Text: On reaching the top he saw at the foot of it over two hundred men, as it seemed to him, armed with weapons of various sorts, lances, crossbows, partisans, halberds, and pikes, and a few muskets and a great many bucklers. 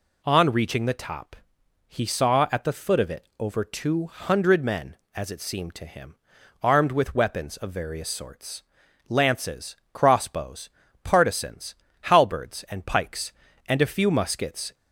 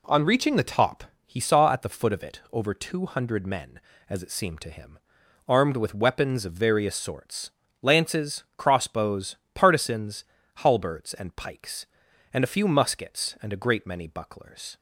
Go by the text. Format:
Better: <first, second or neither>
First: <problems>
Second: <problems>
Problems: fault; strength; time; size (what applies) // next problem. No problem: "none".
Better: second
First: pauses between "top" and "he"; noticeable; at 1.3 s; 0.54 s long // stops before "and a great many bucklers"; at 14.7 s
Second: pauses between "top" and "he"; slight; at 1.0 s; 0.20 s long